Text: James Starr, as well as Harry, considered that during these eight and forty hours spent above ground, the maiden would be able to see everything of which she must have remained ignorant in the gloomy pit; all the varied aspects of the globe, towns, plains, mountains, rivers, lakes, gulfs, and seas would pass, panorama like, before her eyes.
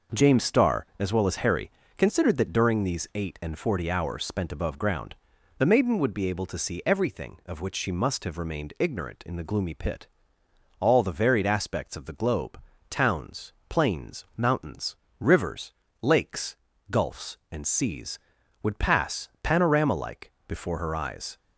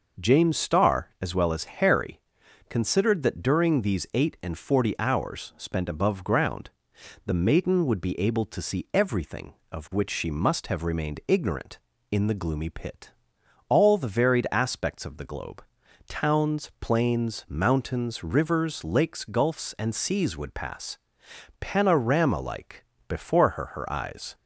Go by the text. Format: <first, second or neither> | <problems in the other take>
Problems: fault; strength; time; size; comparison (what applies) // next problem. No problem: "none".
first | says "her" twice; at 23.6 s